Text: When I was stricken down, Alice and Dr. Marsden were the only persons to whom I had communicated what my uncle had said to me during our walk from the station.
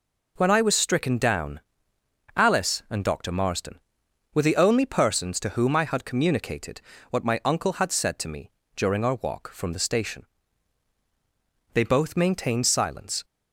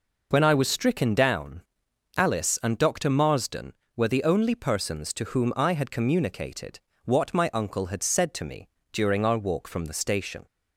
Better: second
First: pauses between "communicated" and "what"; slight; at 6.8 s; 0.26 s long // pauses between "me" and "during"; slight; at 8.5 s; 0.24 s long // goes on to say "They both maintained silence"; from 11.7 s on; 1.5 s long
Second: pauses between "communicated" and "what"; slight; at 6.7 s; 0.24 s long // pauses between "me" and "during"; slight; at 8.6 s; 0.24 s long

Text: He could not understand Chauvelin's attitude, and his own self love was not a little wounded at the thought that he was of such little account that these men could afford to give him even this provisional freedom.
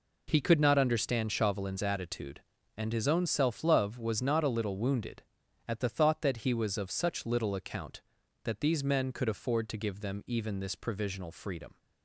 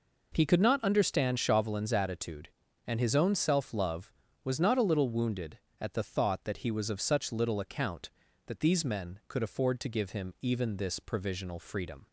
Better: second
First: says "them" for "him"; at 10.0 s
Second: none

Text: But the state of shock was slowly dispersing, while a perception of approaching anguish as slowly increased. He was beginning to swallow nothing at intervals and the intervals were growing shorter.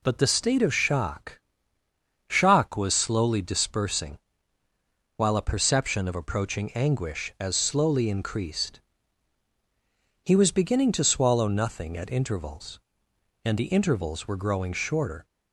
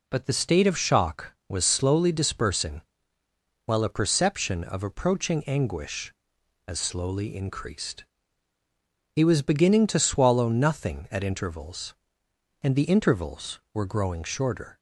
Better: second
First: says "shock" twice; at 2.2 s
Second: none

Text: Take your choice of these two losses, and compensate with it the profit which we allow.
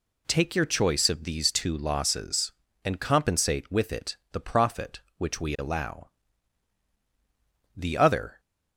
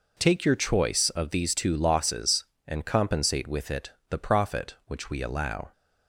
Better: second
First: pauses between "it" and "the"; slight; at 4.1 s; 0.16 s long // goes on to say "The other"; noticeable; from 7.7 s on; 0.64 s long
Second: pauses between "it" and "the"; slight; at 3.8 s; 0.18 s long

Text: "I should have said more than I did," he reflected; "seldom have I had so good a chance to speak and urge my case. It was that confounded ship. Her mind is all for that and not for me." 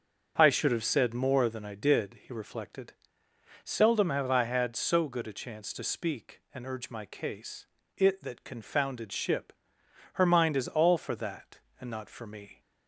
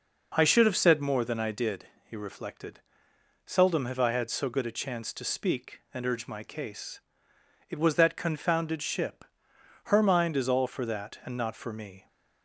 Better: second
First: starts louder than the rest; until 1.3 s; 6.5 dB // skips "was"; at 8.2 s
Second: none

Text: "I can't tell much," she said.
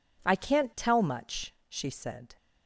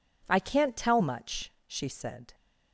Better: neither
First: none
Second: none

